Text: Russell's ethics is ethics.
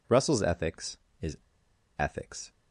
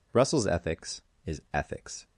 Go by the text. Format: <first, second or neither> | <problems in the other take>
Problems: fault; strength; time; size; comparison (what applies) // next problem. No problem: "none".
second | pauses between "is" and "ethics"; noticeable; at 1.3 s; 0.60 s long